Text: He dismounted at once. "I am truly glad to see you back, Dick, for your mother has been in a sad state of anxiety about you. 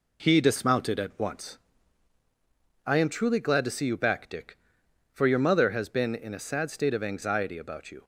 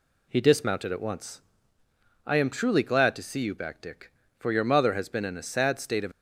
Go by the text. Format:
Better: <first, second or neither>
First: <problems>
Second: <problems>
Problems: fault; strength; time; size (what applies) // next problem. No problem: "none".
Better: first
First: none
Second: stops before "anxiety about you"; at 6.1 s